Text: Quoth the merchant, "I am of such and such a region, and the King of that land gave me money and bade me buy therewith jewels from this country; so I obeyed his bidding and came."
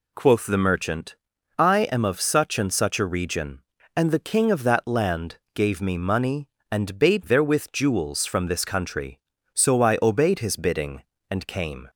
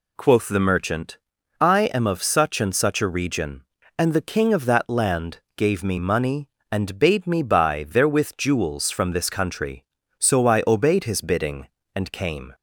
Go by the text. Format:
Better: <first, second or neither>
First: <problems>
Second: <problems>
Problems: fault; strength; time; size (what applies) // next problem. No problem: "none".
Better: second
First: pauses between "land" and "gave"; slight; at 5.3 s; 0.18 s long // skips "me buy"; at 7.2 s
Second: pauses between "land" and "gave"; slight; at 5.3 s; 0.18 s long